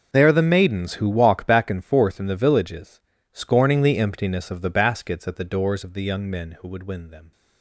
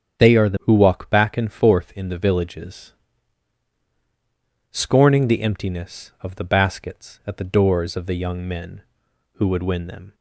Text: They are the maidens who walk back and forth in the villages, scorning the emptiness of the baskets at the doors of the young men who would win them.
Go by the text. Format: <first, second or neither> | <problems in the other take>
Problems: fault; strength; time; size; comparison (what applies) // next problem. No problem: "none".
first | starts louder than the rest; strong; until 1.2 s; 7.5 dB // skips "maidens"; at 0.5 s